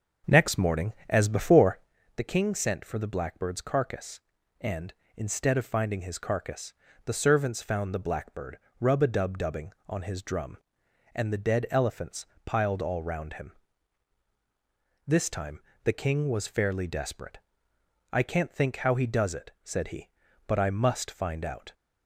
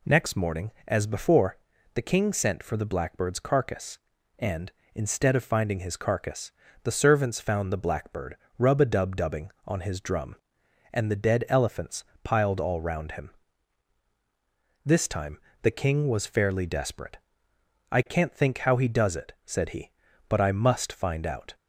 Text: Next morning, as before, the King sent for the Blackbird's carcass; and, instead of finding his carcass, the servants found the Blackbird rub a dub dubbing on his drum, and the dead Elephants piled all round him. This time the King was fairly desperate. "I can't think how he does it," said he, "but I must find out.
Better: second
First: starts louder than the rest; until 2.0 s; 6.5 dB // pauses between "Blackbird" and "rub"; slight; at 8.5 s; 0.22 s long // pauses between "Elephants" and "piled"; slight; at 12.2 s; 0.20 s long // pauses between "time" and "the"; slight; at 15.5 s; 0.24 s long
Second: pauses between "Blackbird" and "rub"; slight; at 8.3 s; 0.22 s long // pauses between "Elephants" and "piled"; slight; at 12.0 s; 0.20 s long // pauses between "time" and "the"; slight; at 15.3 s; 0.24 s long

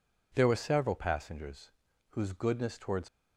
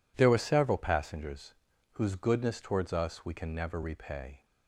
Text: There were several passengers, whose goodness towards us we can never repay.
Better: second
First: stops before "us we can never repay"; at 3.0 s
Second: none

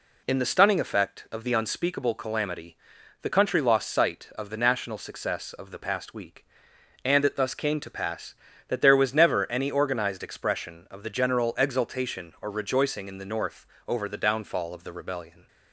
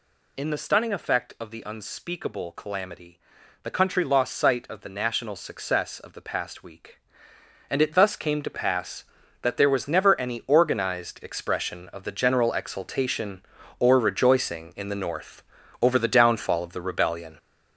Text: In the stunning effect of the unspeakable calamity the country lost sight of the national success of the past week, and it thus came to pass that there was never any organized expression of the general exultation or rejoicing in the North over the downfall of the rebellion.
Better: first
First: pauses between "calamity" and "the"; noticeable; at 2.7 s; 0.46 s long // pauses between "North" and "over"; slight; at 13.6 s; 0.20 s long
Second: gets louder; throughout; 6 dB // pauses between "calamity" and "the"; at 3.1 s; 0.44 s long // pauses between "North" and "over"; at 15.4 s; 0.40 s long

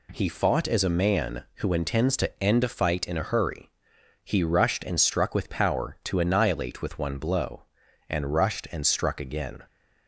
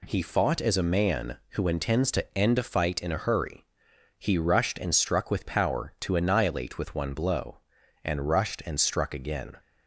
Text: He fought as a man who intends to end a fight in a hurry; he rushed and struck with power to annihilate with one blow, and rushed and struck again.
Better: neither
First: none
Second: none

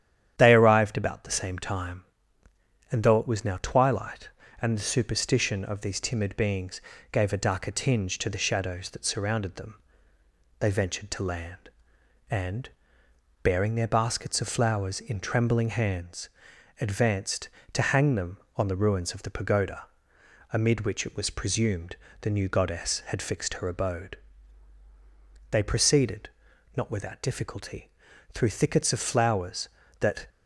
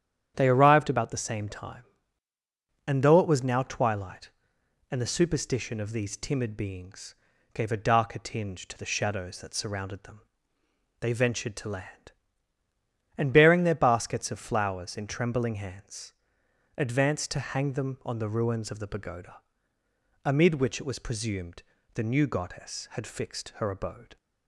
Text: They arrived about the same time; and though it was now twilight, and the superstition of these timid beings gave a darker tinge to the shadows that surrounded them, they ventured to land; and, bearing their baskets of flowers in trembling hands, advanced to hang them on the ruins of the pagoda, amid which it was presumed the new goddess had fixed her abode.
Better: second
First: starts louder than the rest; strong; until 1.3 s; 10 dB // pauses between "beings" and "gave"; slight; at 6.8 s; 0.30 s long // pauses between "presumed" and "the"; slight; at 21.9 s; 0.26 s long // goes on to say "They proceeded not without difficulty through thickets of flowers that"; strong; from 25.5 s on; 4.7 s long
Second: starts louder than the rest; strong; until 1.3 s; 9.5 dB // pauses between "beings" and "gave"; at 7.1 s; 0.38 s long // pauses between "presumed" and "the"; slight; at 21.6 s; 0.30 s long

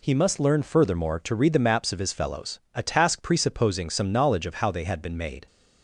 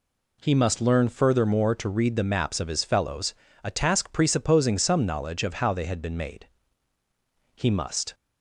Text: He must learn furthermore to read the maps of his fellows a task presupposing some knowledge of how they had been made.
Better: first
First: none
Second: pauses between "fellows" and "a"; slight; at 3.3 s; 0.30 s long // goes on to say "He must"; from 7.5 s on; 0.58 s long

